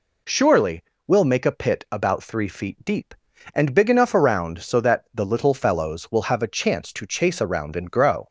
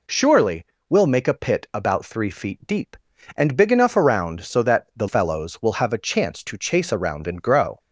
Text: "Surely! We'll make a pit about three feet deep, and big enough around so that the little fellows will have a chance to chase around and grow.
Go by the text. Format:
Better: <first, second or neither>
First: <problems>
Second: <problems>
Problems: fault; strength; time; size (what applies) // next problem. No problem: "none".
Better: first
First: none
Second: skips "little"; at 5.0 s